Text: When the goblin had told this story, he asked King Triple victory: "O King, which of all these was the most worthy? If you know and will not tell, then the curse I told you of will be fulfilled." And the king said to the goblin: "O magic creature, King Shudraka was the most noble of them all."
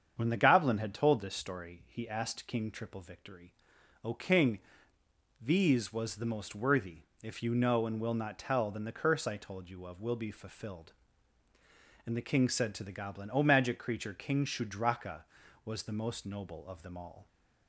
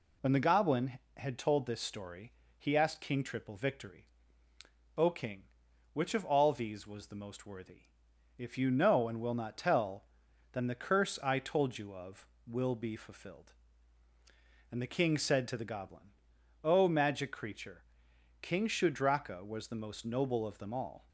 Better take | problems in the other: second | starts louder than the rest; strong; until 1.1 s; 7.5 dB // skips "which of all"; at 4.9 s

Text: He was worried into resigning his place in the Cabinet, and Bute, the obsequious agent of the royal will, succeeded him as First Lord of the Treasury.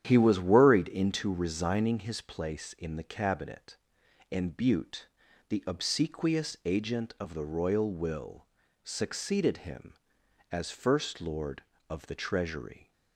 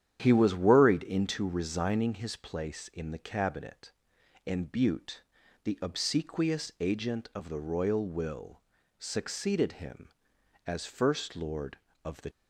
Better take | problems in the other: first | starts louder than the rest; strong; until 1.2 s; 9.5 dB; strong in the first // stops before "Treasury"; at 12.3 s

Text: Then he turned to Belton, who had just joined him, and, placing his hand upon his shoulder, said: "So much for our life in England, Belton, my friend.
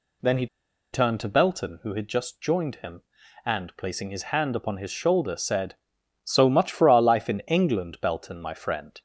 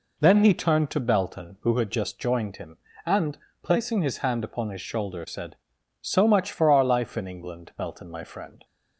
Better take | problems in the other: second | pauses between "he" and "turned"; noticeable; at 0.4 s; 0.47 s long

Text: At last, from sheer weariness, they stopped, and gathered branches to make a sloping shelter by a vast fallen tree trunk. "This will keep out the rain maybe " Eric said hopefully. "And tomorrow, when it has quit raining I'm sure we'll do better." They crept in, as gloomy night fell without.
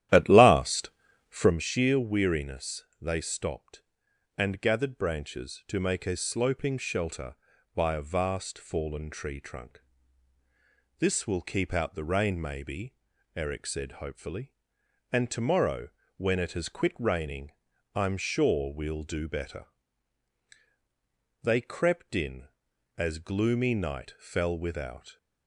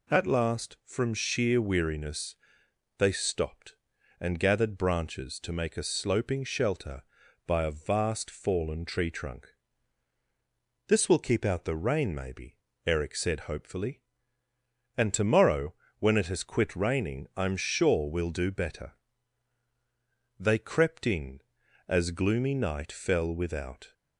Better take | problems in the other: second | starts louder than the rest; strong; until 1.6 s; 12.5 dB // pauses between "raining" and "I'm"; at 17.5 s; 0.42 s long

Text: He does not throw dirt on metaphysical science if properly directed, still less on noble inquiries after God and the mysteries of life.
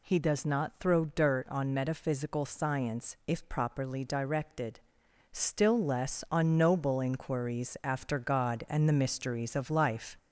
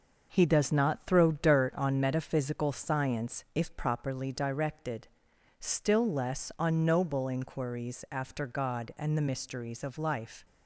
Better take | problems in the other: second | gets louder; slight; throughout; 3 dB

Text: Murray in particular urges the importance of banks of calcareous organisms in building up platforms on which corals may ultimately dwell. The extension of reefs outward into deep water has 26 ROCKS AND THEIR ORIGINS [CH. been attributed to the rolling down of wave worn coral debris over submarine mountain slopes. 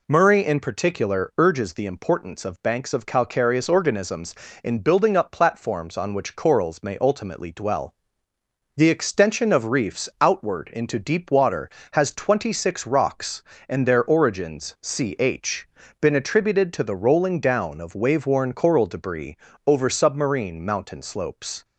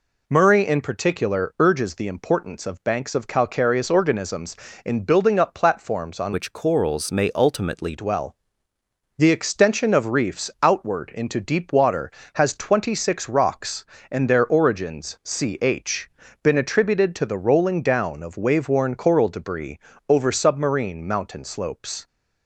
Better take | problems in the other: first | changes voice from "which" to "ultimately"; from 6.3 to 7.9 s; 1.6 s long // pauses between "debris" and "over"; slight; at 19.7 s; 0.32 s long; slight in the first

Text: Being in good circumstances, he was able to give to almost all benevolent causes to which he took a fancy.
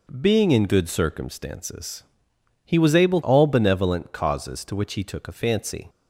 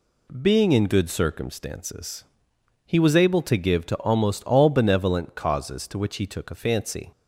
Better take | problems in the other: second | skips "to give to almost"; at 3.2 s

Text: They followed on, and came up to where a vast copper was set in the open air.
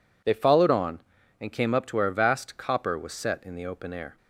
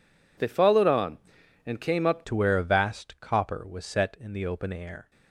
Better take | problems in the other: first | changes voice at "to"; from 2.2 s on; 2.9 s long

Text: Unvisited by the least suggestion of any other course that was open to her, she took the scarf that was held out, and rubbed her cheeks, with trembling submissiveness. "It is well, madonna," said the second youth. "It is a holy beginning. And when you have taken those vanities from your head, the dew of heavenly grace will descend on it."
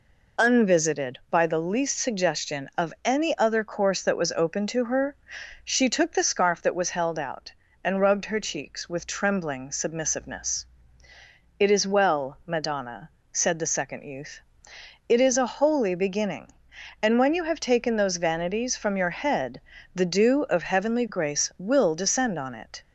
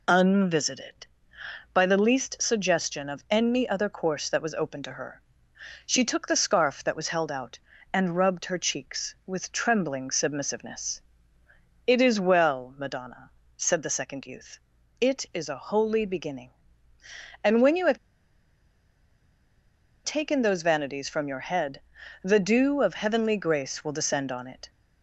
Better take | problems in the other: first | pauses between "have" and "taken"; strong; at 17.9 s; 2.0 s long

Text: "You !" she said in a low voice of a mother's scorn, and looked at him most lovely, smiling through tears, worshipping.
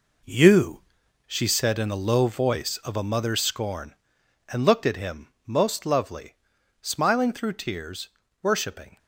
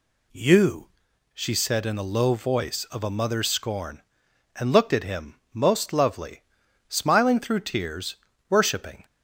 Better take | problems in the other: second | gets quieter; slight; throughout; 2.5 dB

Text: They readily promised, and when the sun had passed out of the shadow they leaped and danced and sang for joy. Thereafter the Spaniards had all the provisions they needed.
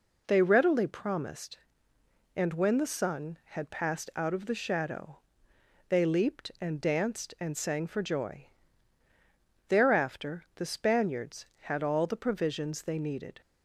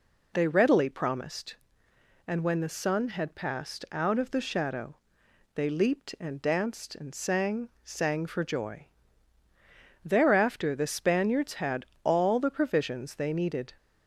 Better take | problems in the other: first | pauses between "shadow" and "they"; noticeable; at 4.9 s; 0.60 s long; noticeable in the first // says "sang" twice; at 7.8 s // pauses between "had" and "all"; slight; at 11.8 s; 0.18 s long

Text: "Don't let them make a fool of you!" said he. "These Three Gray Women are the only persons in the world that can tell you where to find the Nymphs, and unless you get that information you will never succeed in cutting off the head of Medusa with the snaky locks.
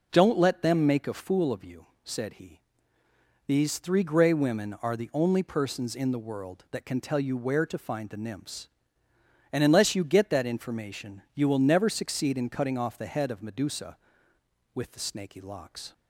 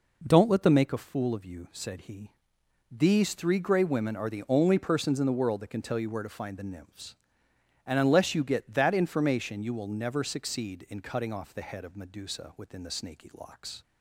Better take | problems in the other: first | says "within" for "with"; at 12.5 s

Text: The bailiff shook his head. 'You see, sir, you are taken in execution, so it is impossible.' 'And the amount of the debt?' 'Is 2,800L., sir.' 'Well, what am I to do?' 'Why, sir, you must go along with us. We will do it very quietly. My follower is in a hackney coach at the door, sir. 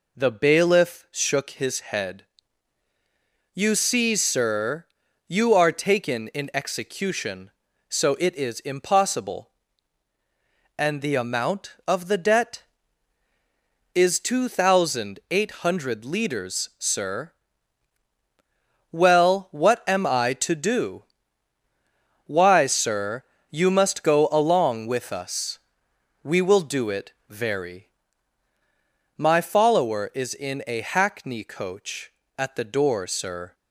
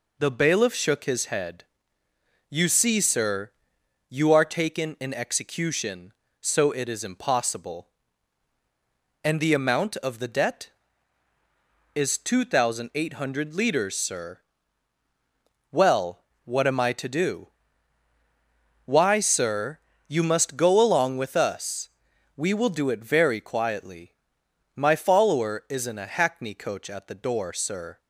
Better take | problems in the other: second | pauses between "it" and "very"; slight; at 27.1 s; 0.18 s long // skips "quietly"; at 28.5 s

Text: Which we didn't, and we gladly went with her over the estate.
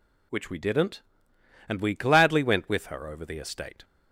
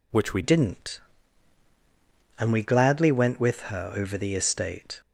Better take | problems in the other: first | changes voice at "didn't"; from 0.4 s on; 4.6 s long

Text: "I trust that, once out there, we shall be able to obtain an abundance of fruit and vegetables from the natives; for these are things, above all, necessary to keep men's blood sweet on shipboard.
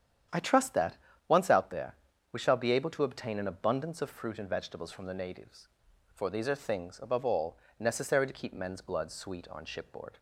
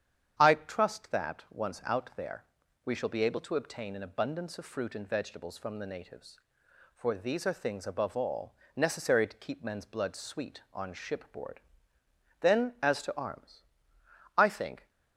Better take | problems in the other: first | starts louder than the rest; strong; until 1.3 s; 8.5 dB; strong in the first // goes on to say "Then as to arms I think"; strong; from 12.4 s on; 2.4 s long

